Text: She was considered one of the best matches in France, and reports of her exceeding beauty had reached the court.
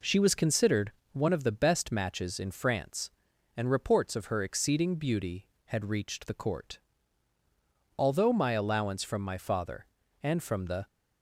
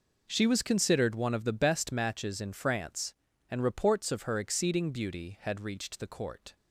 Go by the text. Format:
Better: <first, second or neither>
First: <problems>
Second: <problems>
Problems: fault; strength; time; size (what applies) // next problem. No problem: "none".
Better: second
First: pauses between "considered" and "one"; slight; at 0.9 s; 0.22 s long // goes on to say "Although my allowance from my father and from the"; strong; from 7.9 s on; 2.8 s long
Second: none